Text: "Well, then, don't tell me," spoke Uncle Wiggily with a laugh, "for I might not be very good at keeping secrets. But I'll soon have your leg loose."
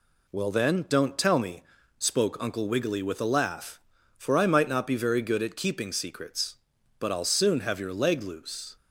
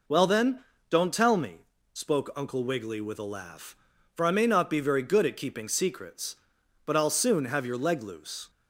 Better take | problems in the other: first | says "may" for "might"; at 4.3 s

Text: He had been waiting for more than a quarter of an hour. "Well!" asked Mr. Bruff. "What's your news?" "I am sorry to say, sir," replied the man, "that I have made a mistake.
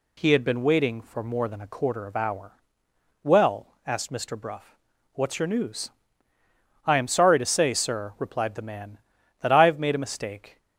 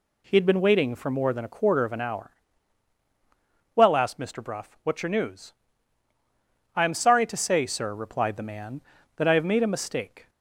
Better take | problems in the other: second | skips "an"; at 2.1 s

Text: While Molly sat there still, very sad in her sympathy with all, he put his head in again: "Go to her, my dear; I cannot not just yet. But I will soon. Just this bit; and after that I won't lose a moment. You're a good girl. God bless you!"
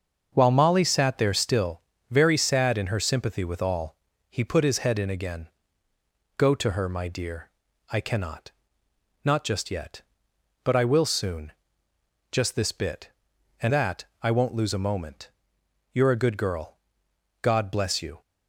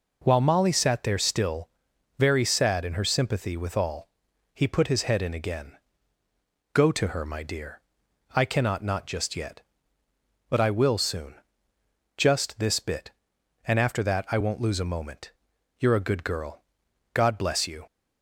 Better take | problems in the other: second | starts louder than the rest; until 1.3 s; 6.5 dB // pauses between "cannot" and "not"; noticeable; at 8.4 s; 0.74 s long // skips "after"; at 13.7 s // pauses between "that" and "I"; slight; at 14.0 s; 0.18 s long

